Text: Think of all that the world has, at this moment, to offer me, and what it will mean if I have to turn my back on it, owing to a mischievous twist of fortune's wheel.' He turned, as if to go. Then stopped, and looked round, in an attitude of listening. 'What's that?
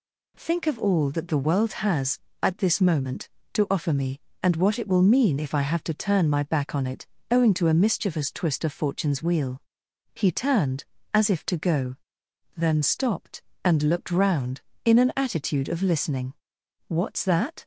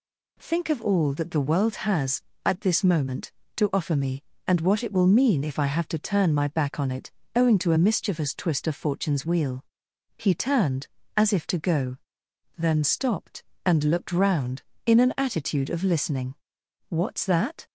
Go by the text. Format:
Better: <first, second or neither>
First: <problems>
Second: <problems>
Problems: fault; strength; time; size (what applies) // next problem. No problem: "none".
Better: neither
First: none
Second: none